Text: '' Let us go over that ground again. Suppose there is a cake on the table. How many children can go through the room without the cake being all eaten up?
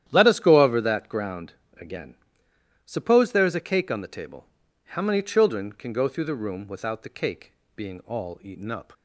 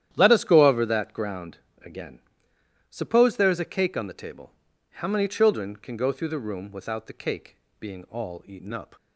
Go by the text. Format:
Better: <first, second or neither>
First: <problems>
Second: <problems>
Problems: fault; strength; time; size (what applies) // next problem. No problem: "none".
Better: neither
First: starts louder than the rest; strong; until 1.0 s; 11 dB // pauses between "ground" and "again"; slight; at 1.5 s; 0.30 s long // pauses between "cake" and "being"; slight; at 7.5 s; 0.20 s long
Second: starts louder than the rest; strong; until 1.1 s; 11 dB // pauses between "ground" and "again"; slight; at 1.5 s; 0.30 s long // pauses between "cake" and "being"; slight; at 7.5 s; 0.20 s long